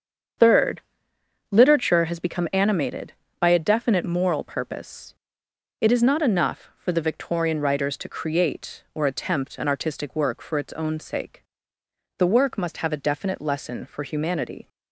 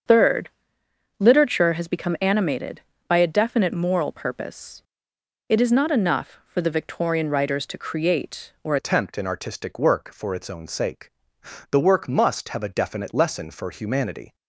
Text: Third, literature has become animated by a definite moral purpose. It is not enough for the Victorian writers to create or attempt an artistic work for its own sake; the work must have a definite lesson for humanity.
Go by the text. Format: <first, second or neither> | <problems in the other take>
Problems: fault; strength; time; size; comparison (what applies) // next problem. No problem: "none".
first | starts louder than the rest; until 1.7 s; 7 dB; strong in the first // changes voice at "attempt"; from 8.7 s on; 5.6 s long